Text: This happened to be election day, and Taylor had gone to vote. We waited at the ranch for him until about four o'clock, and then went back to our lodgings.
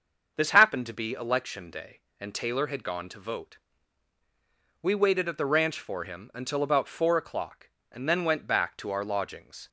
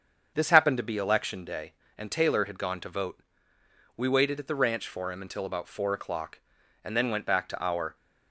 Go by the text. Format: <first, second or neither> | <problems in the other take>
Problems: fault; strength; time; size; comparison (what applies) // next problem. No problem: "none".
first | starts louder than the rest; until 1.3 s; 7 dB; also in the first // stops before "lodgings"; at 7.9 s